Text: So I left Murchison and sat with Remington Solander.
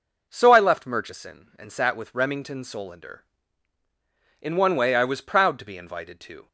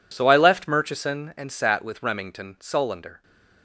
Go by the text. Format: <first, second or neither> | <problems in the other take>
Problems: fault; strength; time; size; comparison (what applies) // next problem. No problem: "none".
second | goes on to say "In one way I was proud to be invited to"; strong; from 4.4 s on; 2.0 s long